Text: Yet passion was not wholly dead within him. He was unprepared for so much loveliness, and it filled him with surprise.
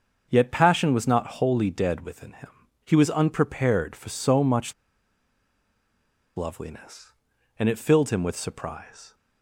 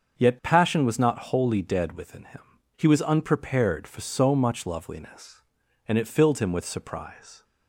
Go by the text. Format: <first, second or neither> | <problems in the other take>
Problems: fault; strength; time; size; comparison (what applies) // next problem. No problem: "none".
second | starts louder than the rest; until 1.3 s; 6.5 dB; also in the second // pauses between "much" and "loveliness"; strong; at 4.7 s; 1.6 s long